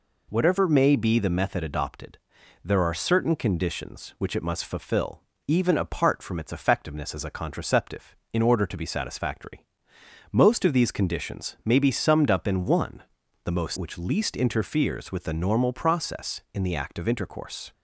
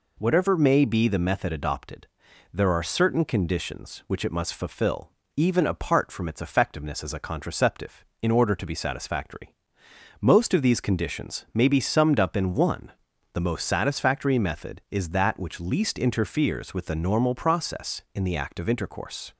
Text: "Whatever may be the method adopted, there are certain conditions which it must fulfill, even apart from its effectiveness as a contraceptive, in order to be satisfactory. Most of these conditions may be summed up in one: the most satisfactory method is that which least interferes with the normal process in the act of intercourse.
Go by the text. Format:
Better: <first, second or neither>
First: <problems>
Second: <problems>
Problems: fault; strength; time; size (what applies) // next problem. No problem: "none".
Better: second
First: skips "satisfactory method is that"; at 13.7 s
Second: none